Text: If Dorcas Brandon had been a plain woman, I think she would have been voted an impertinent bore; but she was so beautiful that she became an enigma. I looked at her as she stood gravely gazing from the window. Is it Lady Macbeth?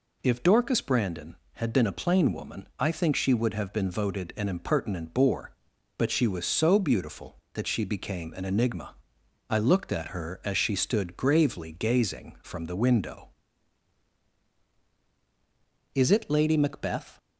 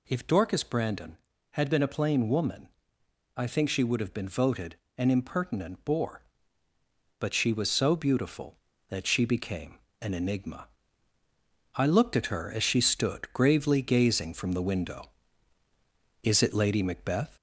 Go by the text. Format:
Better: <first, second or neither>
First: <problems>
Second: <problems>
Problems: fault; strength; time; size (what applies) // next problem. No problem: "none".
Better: first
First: none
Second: gets louder; slight; throughout; 2.5 dB // pauses between "voted" and "an"; slight; at 4.7 s; 0.20 s long // pauses between "became" and "an"; slight; at 9.7 s; 0.20 s long